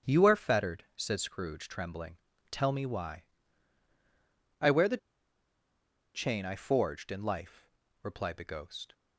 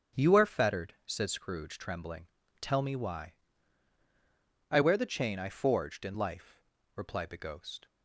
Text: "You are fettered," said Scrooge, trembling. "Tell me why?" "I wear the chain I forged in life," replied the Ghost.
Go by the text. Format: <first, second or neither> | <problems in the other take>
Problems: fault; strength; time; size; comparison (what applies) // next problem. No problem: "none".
second | starts louder than the rest; strong; until 1.1 s; 8 dB; strong in the second // pauses between "the" and "chain"; at 4.9 s; 1.1 s long